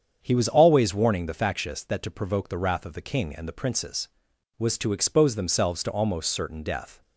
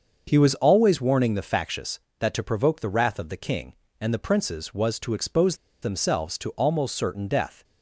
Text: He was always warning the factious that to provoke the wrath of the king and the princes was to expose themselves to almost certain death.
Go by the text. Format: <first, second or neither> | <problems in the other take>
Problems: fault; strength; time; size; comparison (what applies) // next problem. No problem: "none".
first | starts louder than the rest; until 1.3 s; 6.5 dB; strong in the first // pauses between "expose" and "themselves"; slight; at 5.5 s; 0.25 s long